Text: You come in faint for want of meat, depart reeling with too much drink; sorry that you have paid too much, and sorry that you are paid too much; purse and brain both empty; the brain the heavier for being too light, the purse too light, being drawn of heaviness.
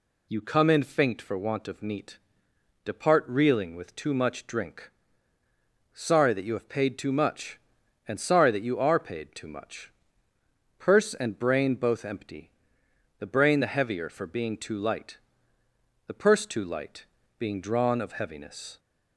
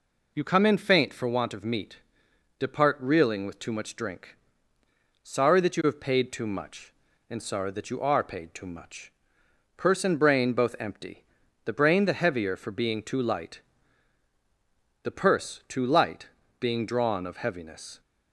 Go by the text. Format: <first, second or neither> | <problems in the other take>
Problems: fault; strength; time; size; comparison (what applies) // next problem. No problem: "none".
neither | none